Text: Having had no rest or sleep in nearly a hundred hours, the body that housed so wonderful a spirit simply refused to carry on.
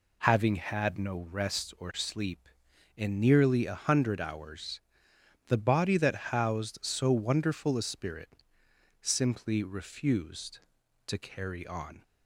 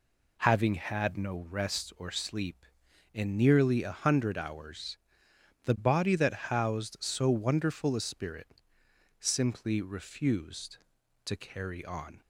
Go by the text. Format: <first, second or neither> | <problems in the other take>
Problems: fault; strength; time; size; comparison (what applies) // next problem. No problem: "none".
neither | pauses between "spirit" and "simply"; noticeable; the same in both